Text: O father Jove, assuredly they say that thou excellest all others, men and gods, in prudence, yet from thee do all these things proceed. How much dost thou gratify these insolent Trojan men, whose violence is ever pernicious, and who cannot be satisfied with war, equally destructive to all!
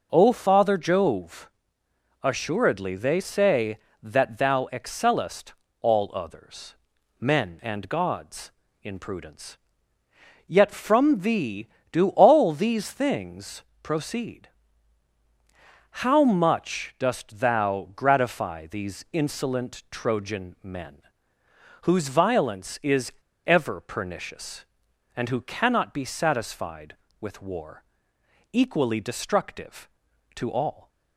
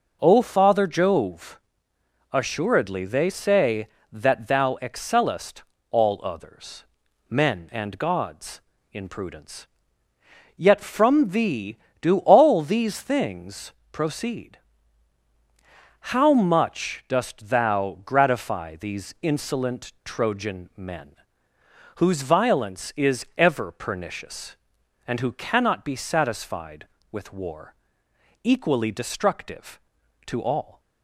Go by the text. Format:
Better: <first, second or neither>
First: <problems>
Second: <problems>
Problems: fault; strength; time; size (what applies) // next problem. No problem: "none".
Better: second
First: pauses between "excellest" and "all"; slight; at 5.5 s; 0.28 s long // pauses between "things" and "proceed"; slight; at 13.6 s; 0.22 s long // pauses between "is" and "ever"; slight; at 23.1 s; 0.34 s long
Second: pauses between "excellest" and "all"; slight; at 5.6 s; 0.28 s long // pauses between "things" and "proceed"; slight; at 13.7 s; 0.22 s long